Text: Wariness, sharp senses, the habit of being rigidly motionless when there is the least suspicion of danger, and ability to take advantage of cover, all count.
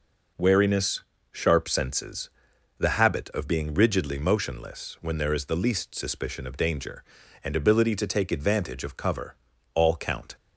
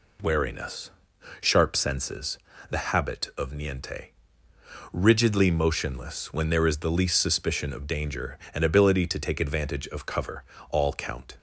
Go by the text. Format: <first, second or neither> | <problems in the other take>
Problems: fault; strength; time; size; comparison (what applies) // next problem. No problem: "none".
first | says "niente" for "being"; at 3.5 s